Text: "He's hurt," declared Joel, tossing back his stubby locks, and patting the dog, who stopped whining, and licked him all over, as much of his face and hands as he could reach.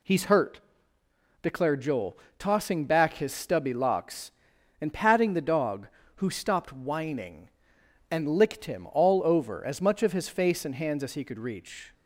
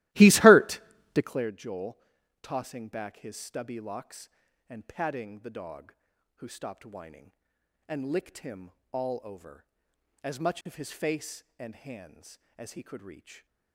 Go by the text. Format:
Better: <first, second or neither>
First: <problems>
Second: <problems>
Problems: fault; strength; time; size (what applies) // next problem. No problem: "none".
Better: first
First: none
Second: starts louder than the rest; strong; until 1.5 s; 17 dB // pauses between "him" and "all"; slight; at 8.7 s; 0.20 s long